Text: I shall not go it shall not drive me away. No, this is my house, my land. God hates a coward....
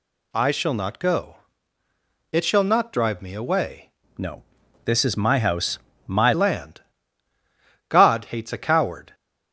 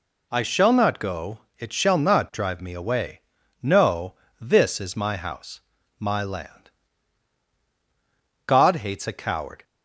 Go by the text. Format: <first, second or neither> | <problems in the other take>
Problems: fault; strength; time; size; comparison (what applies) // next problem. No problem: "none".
second | pauses between "go" and "it"; noticeable; at 1.3 s; 0.94 s long; slight in the second // changes voice from "No" to "my"; from 4.1 to 6.3 s; 2.2 s long